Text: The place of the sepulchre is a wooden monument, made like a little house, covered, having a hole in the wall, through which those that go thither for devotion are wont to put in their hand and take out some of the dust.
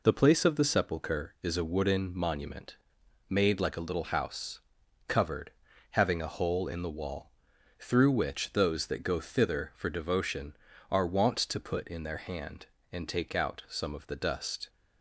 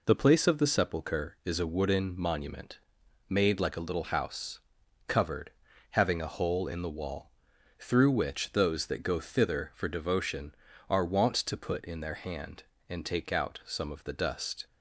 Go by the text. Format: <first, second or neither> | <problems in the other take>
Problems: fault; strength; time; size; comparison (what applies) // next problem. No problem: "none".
neither | none